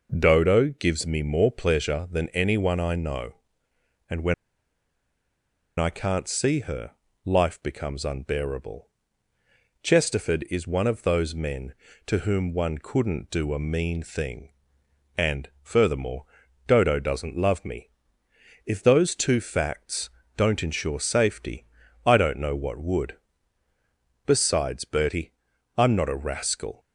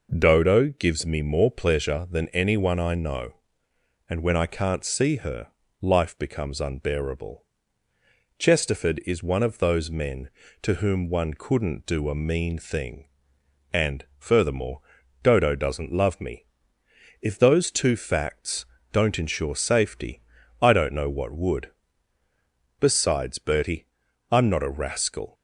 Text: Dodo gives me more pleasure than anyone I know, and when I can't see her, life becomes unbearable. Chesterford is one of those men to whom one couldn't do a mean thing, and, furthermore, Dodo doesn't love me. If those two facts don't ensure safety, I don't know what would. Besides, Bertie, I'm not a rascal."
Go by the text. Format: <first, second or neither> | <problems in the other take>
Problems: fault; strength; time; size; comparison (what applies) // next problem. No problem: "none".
second | pauses between "when" and "I"; strong; at 4.3 s; 1.4 s long // pauses between "facts" and "don't"; slight; at 20.0 s; 0.26 s long; slight in the second